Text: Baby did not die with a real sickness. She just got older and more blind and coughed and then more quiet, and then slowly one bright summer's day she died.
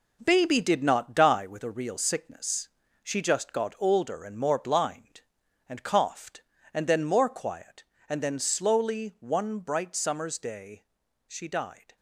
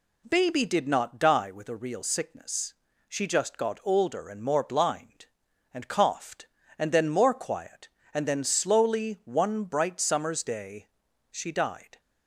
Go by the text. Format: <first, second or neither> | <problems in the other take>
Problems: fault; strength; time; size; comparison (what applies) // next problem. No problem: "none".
second | gets quieter; strong; throughout; 8.5 dB // pauses between "day" and "she"; at 10.8 s; 0.42 s long; also in the second